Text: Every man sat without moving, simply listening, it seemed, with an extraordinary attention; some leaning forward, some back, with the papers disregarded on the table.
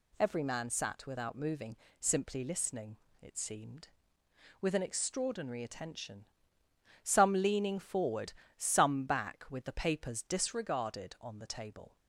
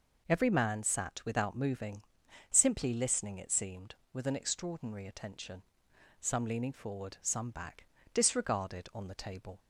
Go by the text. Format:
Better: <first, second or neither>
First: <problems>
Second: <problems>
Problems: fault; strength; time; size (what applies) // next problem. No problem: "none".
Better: first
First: none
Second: skips "with the papers"; at 7.9 s